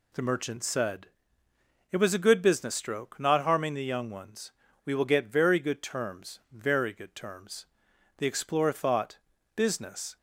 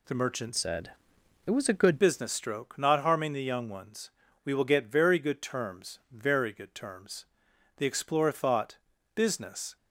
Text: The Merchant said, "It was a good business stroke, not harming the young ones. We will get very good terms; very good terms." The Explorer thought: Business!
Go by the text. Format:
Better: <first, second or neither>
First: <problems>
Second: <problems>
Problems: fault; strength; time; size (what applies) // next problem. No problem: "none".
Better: first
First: none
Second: changes voice from "said" to "good"; from 0.5 to 2.0 s; 1.5 s long